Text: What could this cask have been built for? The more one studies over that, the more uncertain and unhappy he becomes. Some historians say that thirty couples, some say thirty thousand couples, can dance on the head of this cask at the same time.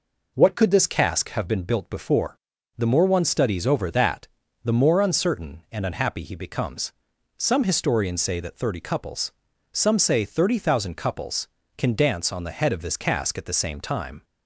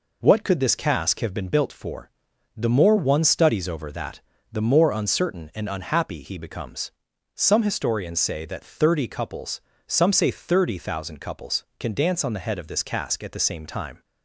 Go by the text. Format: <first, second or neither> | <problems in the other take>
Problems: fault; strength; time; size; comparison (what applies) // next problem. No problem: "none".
second | says "before" for "for"; at 1.8 s